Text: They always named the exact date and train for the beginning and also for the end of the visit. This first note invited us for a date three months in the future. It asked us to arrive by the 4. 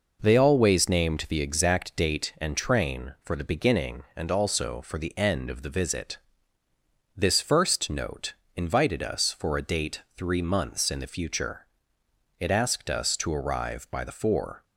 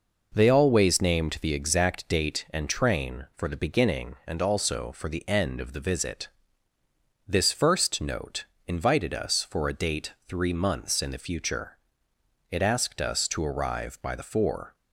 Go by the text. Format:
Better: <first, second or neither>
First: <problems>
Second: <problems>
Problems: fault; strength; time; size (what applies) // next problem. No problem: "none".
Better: neither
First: pauses between "note" and "invited"; slight; at 8.3 s; 0.20 s long // pauses between "date" and "three"; slight; at 10.0 s; 0.16 s long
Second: pauses between "note" and "invited"; slight; at 8.4 s; 0.20 s long // pauses between "date" and "three"; slight; at 10.1 s; 0.16 s long